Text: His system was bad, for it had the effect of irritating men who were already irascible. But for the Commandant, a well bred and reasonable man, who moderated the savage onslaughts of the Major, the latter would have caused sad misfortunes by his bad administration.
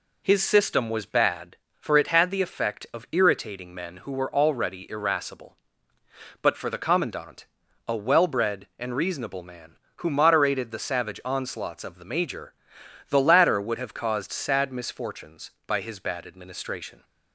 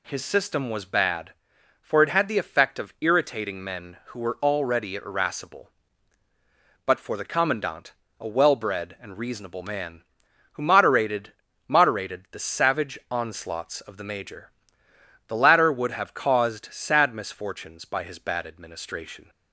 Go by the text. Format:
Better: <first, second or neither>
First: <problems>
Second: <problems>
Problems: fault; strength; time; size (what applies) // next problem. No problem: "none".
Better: first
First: none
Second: says "moderated" twice; at 11.6 s